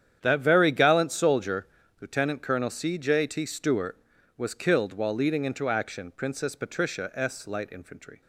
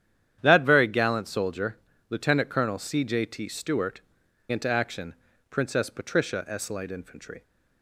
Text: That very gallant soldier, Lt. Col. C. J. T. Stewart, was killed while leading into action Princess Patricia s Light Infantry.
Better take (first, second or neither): first